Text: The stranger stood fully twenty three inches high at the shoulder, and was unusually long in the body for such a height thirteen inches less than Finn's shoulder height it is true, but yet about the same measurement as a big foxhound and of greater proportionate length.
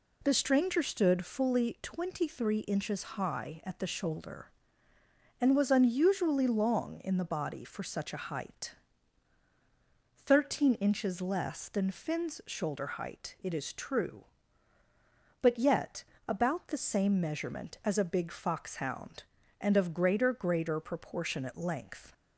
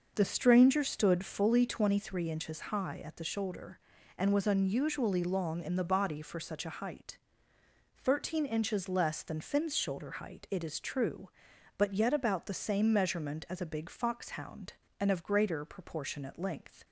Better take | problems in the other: second | pauses between "height" and "thirteen"; strong; at 8.7 s; 1.5 s long; noticeable in the second // pauses between "yet" and "about"; slight; at 16.0 s; 0.24 s long // says "greater" twice; at 20.3 s

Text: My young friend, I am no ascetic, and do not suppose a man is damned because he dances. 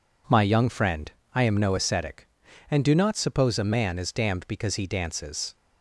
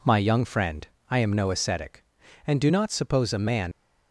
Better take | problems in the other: first | stops before "is damned because he dances"; at 3.7 s

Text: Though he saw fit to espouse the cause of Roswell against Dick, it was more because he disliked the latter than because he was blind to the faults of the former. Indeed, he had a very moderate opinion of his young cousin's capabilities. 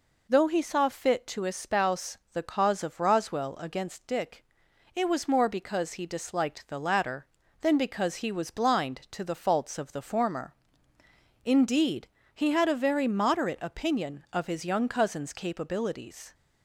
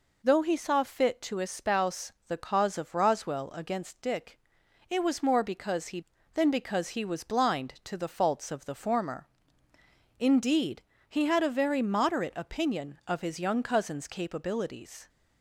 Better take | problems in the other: first | skips "disliked the latter"; at 6.1 s

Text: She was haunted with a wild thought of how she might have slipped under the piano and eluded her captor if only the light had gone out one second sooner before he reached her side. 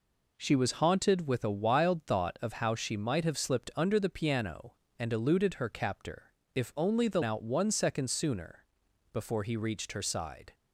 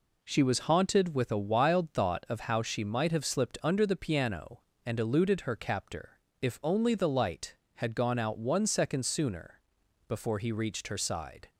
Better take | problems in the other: second | pauses between "captor" and "if"; slight; at 6.3 s; 0.22 s long; slight in the second // skips "light had gone"; at 7.2 s // pauses between "sooner" and "before"; noticeable; at 8.6 s; 0.48 s long; noticeable in the second

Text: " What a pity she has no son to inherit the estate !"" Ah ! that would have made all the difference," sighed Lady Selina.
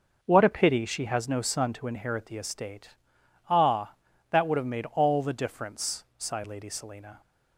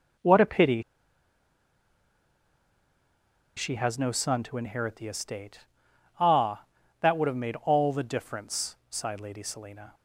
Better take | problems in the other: first | pauses between "pity" and "she"; strong; at 0.8 s; 2.7 s long

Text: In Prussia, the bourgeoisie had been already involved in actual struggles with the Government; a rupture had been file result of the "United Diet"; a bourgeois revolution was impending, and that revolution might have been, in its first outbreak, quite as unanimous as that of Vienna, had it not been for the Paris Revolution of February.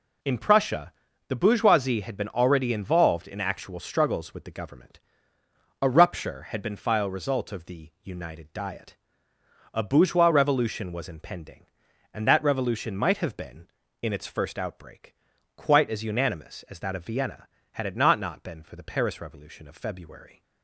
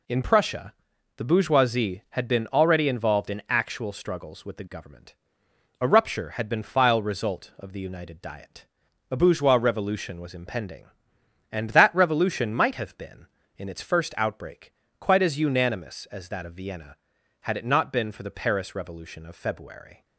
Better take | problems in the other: second | says "not" twice; at 18.1 s

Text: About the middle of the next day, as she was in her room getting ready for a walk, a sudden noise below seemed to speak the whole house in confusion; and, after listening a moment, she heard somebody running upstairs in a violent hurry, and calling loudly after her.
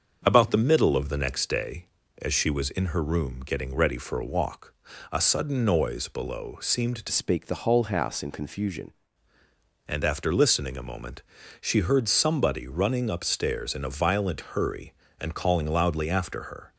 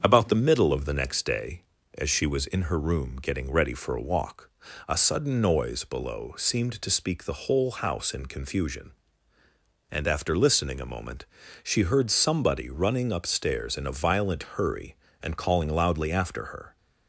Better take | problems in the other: second | starts louder than the rest; until 1.2 s; 6.5 dB; strong in the second // changes voice from "speak" to "confusion"; from 7.1 to 8.9 s; 1.8 s long

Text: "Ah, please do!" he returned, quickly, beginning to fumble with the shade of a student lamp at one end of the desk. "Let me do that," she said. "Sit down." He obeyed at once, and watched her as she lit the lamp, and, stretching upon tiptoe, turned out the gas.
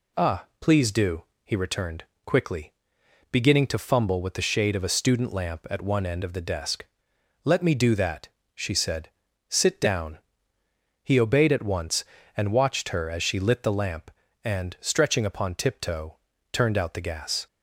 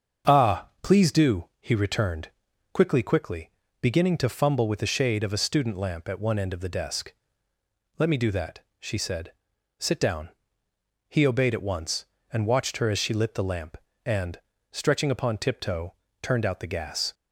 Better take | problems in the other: first | starts louder than the rest; until 1.4 s; 7 dB // says "quickly" twice; at 3.0 s

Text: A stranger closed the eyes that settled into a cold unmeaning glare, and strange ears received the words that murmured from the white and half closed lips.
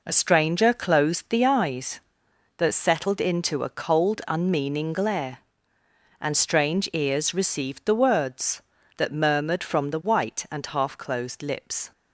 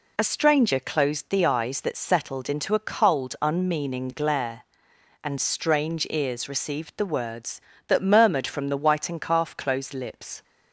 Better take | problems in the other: first | says "calf" for "half"; at 9.2 s

